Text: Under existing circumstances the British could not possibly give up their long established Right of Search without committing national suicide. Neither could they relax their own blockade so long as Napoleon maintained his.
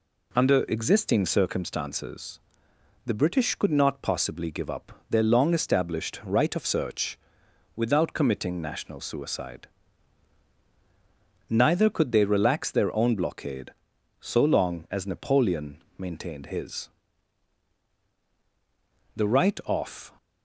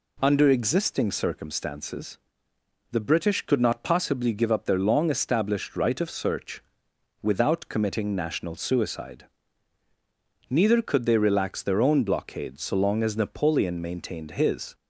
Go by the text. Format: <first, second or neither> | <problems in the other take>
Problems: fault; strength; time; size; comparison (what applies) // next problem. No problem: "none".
second | pauses between "circumstances" and "the"; noticeable; at 2.3 s; 0.64 s long; noticeable in the second // pauses between "up" and "their"; slight; at 4.9 s; 0.18 s long // pauses between "Search" and "without"; noticeable; at 7.1 s; 0.58 s long; noticeable in the second // pauses between "Napoleon" and "maintained"; slight; at 15.8 s; 0.16 s long // goes on to say "The Right of"; noticeable; from 19.1 s on; 0.98 s long